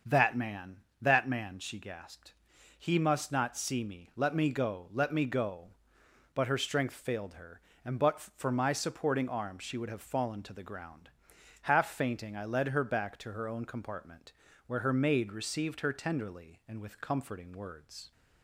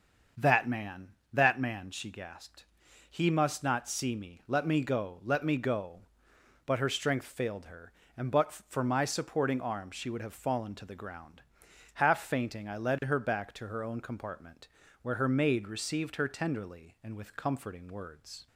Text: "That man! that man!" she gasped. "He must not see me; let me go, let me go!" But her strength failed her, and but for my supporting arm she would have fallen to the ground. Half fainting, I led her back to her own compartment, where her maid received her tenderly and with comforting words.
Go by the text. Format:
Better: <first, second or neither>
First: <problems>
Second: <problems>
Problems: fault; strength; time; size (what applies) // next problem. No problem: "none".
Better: neither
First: starts louder than the rest; until 1.2 s; 6.5 dB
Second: starts louder than the rest; until 1.6 s; 6.5 dB